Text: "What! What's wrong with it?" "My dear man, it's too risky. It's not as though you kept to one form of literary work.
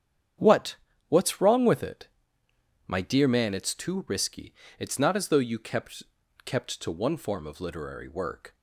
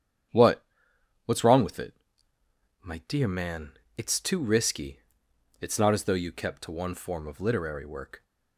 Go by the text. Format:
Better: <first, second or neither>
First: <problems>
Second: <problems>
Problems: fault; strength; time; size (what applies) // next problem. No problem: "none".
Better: second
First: starts louder than the rest; strong; until 1.7 s; 9 dB // says "kept" twice; at 6.4 s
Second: starts louder than the rest; strong; until 1.9 s; 8.5 dB